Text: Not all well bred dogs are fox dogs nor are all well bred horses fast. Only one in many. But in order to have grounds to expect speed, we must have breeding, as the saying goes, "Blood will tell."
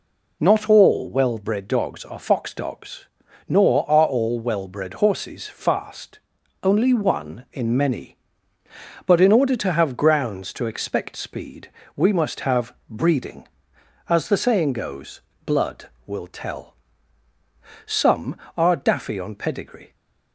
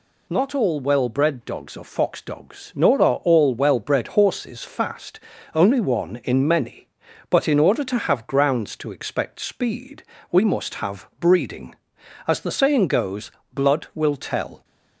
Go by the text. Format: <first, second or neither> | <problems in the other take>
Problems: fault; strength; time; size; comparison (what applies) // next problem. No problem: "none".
second | pauses between "dogs" and "nor"; at 3.0 s; 0.42 s long // pauses between "have" and "breeding"; slight; at 12.7 s; 0.16 s long // goes on to say "Some are daffy on pedigree"; strong; from 17.8 s on; 2.0 s long